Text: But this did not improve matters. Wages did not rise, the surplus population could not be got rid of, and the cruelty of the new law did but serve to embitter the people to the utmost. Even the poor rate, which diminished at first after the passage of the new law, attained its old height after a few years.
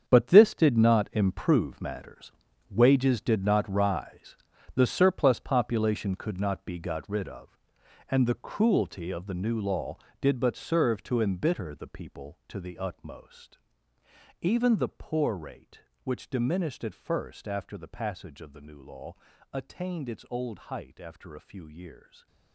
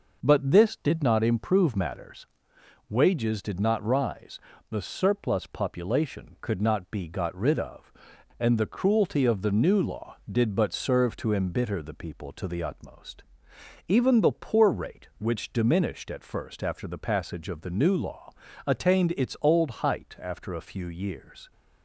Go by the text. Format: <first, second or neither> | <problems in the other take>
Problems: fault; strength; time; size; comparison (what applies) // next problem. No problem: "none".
second | gets quieter; strong; throughout; 12.5 dB // stays silent after the last word; slight; from 21.9 s on; 0.6 s long